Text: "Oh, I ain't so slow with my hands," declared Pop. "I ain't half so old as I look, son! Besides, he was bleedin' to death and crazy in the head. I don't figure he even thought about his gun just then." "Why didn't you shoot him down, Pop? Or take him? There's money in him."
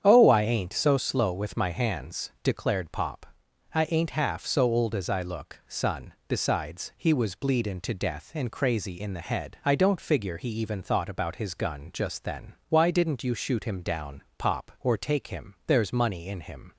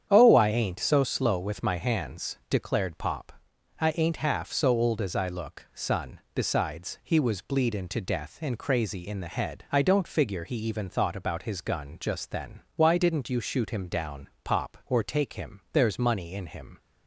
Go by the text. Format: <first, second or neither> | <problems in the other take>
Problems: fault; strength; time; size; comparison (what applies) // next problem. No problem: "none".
neither | starts louder than the rest; strong; the same in both